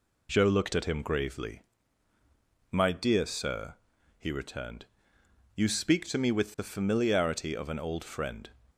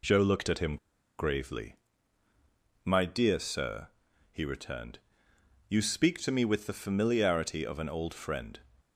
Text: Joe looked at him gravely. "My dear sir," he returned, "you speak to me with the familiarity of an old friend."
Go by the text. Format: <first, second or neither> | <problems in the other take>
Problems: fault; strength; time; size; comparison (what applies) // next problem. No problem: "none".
first | pauses between "him" and "gravely"; at 0.7 s; 0.42 s long